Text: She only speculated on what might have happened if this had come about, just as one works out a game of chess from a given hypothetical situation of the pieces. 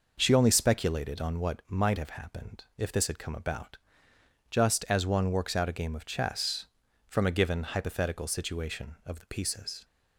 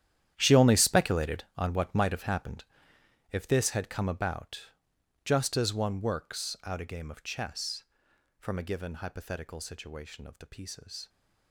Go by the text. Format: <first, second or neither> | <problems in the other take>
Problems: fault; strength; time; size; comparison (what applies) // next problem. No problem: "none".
first | gets quieter; strong; throughout; 15.5 dB // pauses between "happened" and "if"; noticeable; at 2.6 s; 0.66 s long